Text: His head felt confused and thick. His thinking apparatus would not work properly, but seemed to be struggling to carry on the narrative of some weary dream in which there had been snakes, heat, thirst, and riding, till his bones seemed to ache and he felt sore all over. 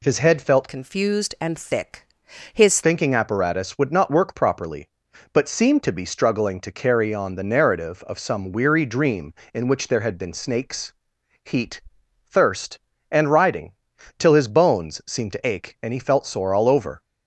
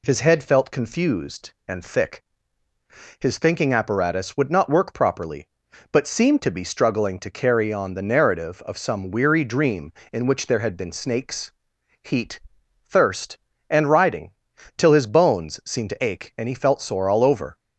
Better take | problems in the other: second | changes voice from "confused" to "His"; from 0.6 to 2.8 s; 2.2 s long

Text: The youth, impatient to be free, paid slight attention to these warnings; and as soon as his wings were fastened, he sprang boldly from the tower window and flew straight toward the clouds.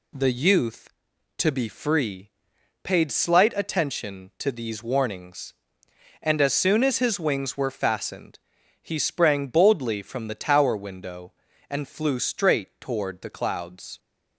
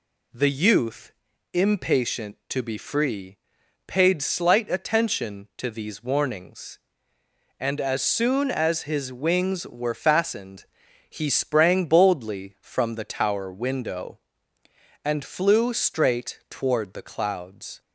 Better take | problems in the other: second | skips "impatient"; at 1.1 s

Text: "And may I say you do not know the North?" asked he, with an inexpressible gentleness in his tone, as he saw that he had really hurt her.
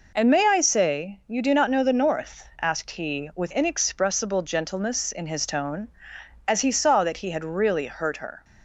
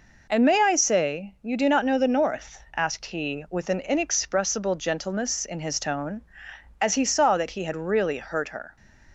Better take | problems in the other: second | skips "an"; at 3.5 s

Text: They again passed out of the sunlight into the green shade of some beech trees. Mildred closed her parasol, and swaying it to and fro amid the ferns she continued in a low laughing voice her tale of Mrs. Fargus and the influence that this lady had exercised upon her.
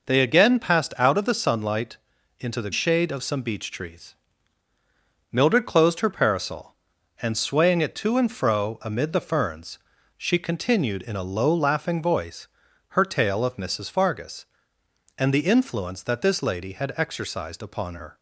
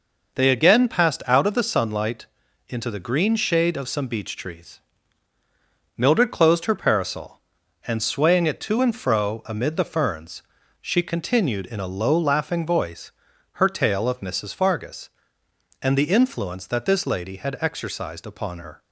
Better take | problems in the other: second | pauses between "sunlight" and "into"; at 1.9 s; 0.42 s long; also in the second // skips "green"; at 2.7 s // pauses between "ferns" and "she"; at 9.7 s; 0.38 s long; also in the second // pauses between "voice" and "her"; at 12.4 s; 0.40 s long; also in the second

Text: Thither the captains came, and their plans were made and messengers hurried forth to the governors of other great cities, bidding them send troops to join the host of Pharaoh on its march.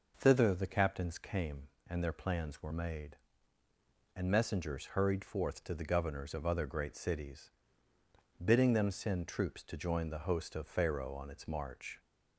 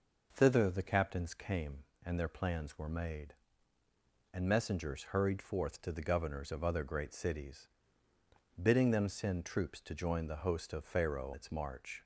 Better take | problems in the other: first | skips "on"; at 11.3 s

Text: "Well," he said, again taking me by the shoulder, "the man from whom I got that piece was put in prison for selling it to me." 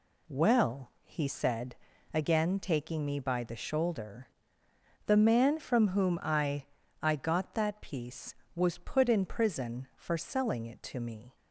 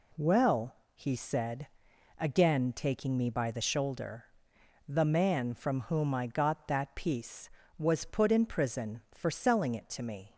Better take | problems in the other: second | says "I" twice; at 6.9 s

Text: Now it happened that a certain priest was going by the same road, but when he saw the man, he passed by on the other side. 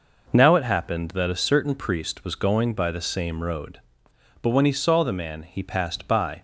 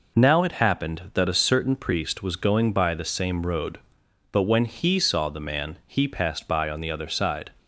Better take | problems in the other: second | stops before "on the other side"; at 6.3 s

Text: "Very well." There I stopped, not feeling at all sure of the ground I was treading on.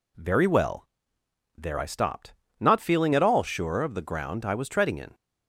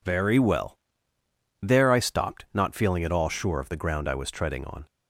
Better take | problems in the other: second | says "in" for "on"; at 4.9 s

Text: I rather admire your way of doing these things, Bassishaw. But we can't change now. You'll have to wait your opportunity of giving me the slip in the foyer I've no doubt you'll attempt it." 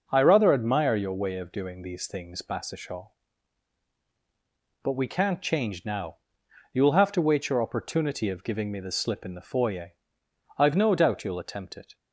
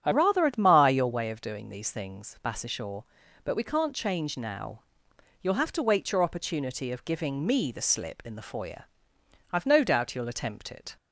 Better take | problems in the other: first | starts louder than the rest; strong; until 1.0 s; 8.5 dB // changes voice at "rather"; from 0.1 s on; 10.8 s long // pauses between "foyer" and "I've"; noticeable; at 8.8 s; 0.66 s long; noticeable in the first

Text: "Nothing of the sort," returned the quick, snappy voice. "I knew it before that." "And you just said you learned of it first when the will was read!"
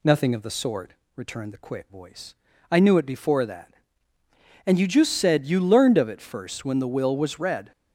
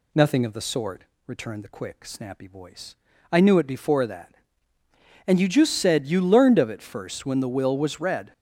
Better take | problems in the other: second | skips "snappy"; at 1.9 s

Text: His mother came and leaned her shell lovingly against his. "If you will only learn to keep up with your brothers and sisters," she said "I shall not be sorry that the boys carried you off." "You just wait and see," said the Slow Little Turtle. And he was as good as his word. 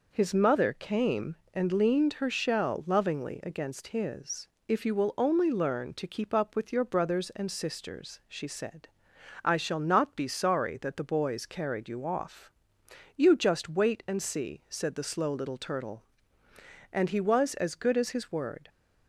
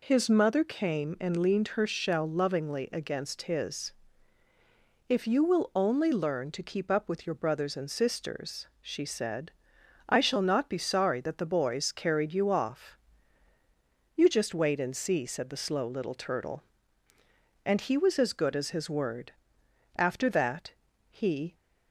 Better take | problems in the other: first | pauses between "said" and "I"; noticeable; at 9.5 s; 0.56 s long; noticeable in the first // goes on to say "After that he"; from 19.9 s on; 1.5 s long

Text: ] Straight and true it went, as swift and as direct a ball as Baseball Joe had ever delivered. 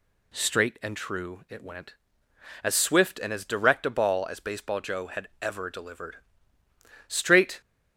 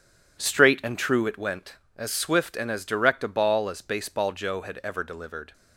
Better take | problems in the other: second | goes on to say "Straight"; from 7.0 s on; 0.54 s long

